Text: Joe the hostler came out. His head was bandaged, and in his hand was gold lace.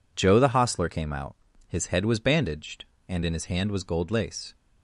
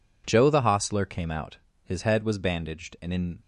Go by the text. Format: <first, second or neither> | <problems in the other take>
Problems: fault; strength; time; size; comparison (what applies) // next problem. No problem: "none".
first | stops before "his hand was gold lace"; at 3.4 s